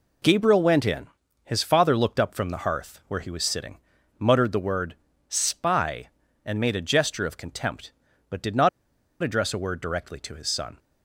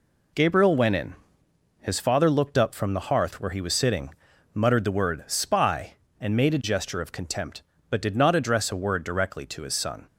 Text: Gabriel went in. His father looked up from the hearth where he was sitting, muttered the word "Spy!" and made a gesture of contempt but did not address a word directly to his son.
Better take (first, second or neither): second